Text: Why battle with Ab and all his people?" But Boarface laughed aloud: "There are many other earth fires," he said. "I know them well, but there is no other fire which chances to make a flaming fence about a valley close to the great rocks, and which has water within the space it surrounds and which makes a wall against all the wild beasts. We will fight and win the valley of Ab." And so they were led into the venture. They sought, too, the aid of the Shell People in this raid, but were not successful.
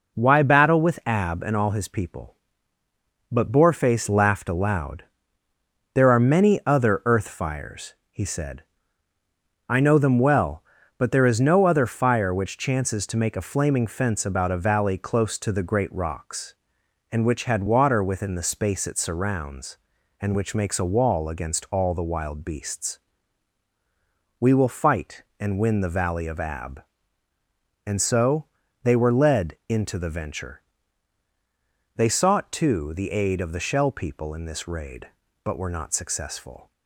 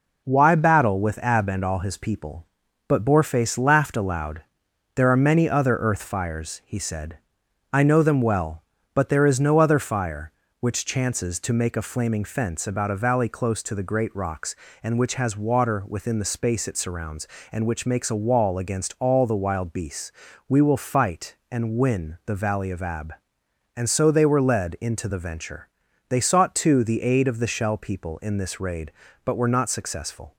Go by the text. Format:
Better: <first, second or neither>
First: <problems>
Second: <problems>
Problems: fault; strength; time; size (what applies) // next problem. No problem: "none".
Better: second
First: says "had" for "has"; at 17.4 s // pauses between "so" and "they"; at 28.4 s; 0.38 s long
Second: none